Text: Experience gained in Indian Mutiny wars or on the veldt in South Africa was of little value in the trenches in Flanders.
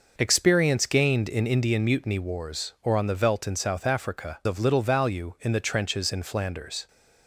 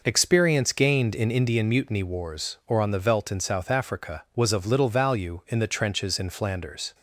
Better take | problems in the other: second | skips "was"; at 4.4 s

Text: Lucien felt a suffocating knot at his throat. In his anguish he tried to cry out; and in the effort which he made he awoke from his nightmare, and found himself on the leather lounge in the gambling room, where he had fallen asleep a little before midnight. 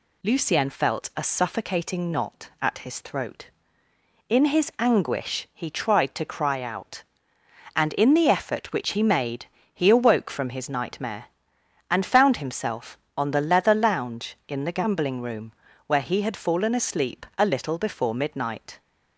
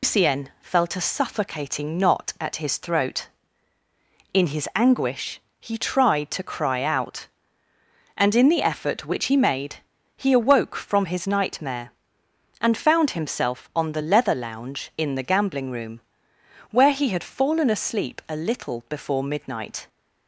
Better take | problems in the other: first | loses the start of "Lucien"; at 0.0 s; 160 ms // pauses between "anguish" and "he"; slight; at 5.3 s; 0.22 s long // pauses between "made" and "he"; at 9.7 s; 0.42 s long; slight in the first

